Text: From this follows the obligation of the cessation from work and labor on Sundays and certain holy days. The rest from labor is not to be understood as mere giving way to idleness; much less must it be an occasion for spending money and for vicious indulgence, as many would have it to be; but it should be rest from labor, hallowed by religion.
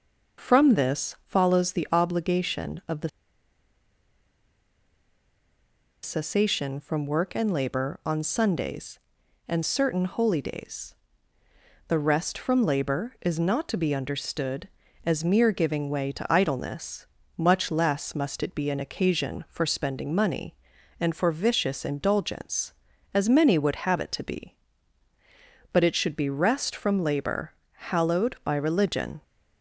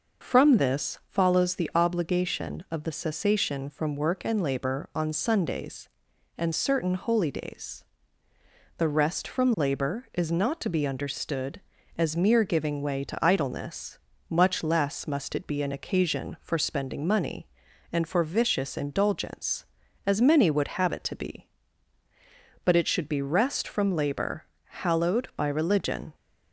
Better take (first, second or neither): second